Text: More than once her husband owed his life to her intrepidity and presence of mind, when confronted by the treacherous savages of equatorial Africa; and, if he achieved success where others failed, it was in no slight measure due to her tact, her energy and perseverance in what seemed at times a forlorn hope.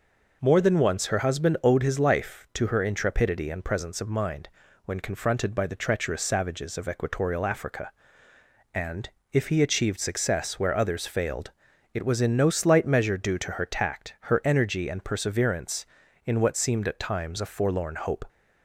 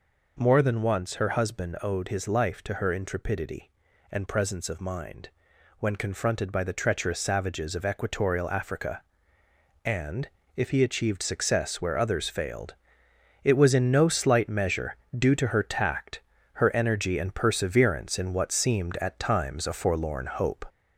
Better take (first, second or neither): first